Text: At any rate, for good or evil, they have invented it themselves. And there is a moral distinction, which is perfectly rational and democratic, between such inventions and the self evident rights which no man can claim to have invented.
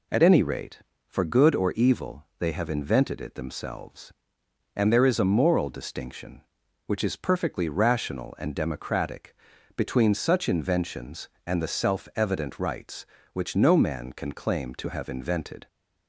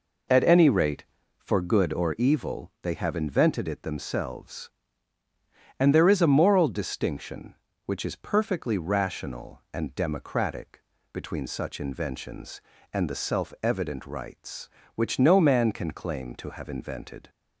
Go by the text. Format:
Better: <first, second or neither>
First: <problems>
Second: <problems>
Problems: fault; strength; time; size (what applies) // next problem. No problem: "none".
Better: neither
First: none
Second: none